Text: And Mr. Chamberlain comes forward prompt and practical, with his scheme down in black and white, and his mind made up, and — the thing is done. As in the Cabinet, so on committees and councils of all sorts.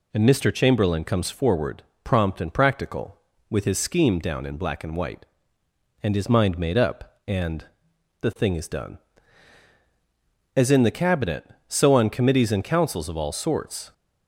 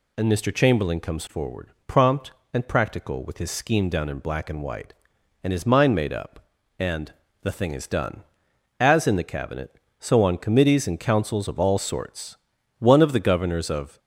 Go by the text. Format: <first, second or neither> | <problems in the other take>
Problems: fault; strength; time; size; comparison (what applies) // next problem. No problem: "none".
first | pauses between "forward" and "prompt"; slight; at 1.7 s; 0.16 s long; slight in the first // goes on to say "One of the governors of"; noticeable; from 12.7 s on; 1.2 s long